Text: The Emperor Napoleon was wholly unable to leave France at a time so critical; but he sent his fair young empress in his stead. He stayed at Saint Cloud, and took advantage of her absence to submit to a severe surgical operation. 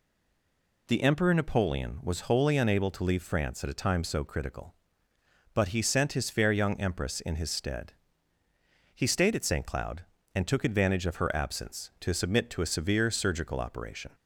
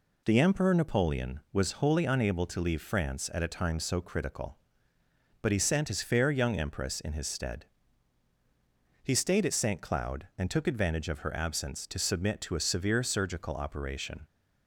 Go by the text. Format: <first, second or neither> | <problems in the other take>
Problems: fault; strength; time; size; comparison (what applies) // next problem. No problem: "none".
second | stays silent before the first word; slight; until 0.8 s; 0.8 s long